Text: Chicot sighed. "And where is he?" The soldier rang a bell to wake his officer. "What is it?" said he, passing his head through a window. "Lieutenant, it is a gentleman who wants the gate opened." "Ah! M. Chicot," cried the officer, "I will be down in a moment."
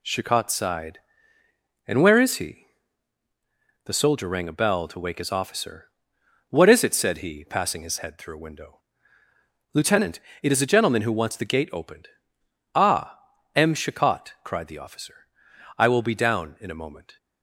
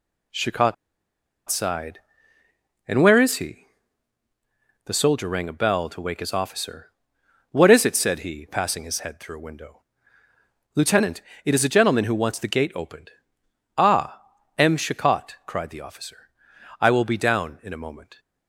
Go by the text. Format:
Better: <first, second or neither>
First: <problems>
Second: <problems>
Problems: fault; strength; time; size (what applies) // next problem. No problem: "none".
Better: first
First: none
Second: pauses between "Chicot" and "sighed"; noticeable; at 0.7 s; 0.74 s long